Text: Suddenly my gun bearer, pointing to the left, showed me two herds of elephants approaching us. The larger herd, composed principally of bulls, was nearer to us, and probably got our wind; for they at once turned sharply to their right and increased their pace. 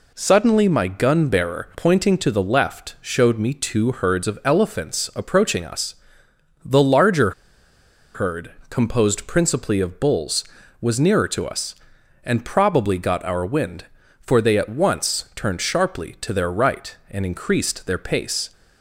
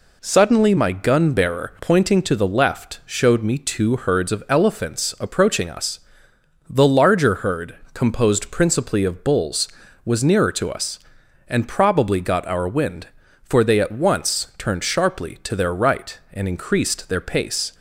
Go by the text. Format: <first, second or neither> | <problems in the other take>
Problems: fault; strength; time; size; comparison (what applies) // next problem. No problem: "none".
second | pauses between "larger" and "herd"; noticeable; at 7.3 s; 0.83 s long